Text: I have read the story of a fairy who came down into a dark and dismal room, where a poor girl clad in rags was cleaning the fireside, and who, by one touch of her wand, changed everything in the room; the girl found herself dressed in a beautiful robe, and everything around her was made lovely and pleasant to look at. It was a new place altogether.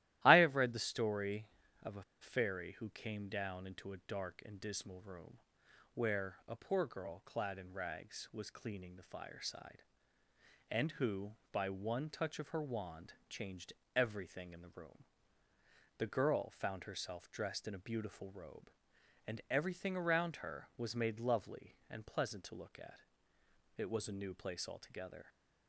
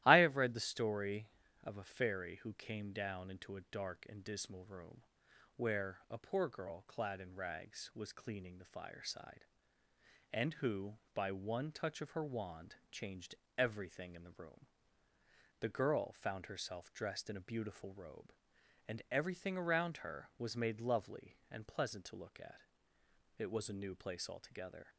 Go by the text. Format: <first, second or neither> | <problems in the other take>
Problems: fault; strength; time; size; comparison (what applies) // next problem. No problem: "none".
second | starts louder than the rest; strong; until 1.2 s; 15 dB; strong in the second // pauses between "a" and "fairy"; slight; at 2.0 s; 0.19 s long // pauses between "changed" and "everything"; slight; at 13.7 s; 0.22 s long; slight in the second